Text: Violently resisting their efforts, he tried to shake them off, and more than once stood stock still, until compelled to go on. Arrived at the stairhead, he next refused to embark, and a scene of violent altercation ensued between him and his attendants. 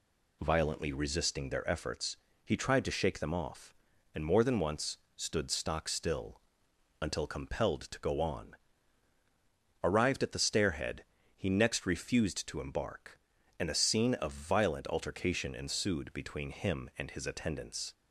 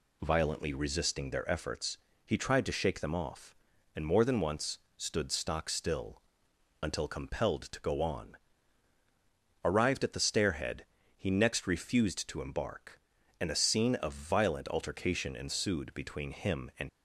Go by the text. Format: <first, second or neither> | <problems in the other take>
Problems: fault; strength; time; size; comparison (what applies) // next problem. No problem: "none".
first | pauses between "once" and "stood"; slight; at 4.7 s; 0.20 s long; slight in the first // stops before "his attendants"; at 16.8 s